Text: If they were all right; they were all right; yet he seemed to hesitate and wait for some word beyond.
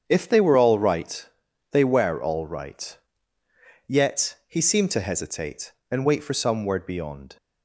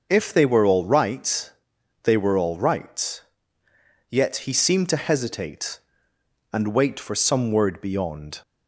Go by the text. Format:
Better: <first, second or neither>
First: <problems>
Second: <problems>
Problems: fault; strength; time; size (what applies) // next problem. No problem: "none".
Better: neither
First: starts louder than the rest; strong; until 1.1 s; 7.5 dB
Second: starts louder than the rest; noticeable; until 1.1 s; 6 dB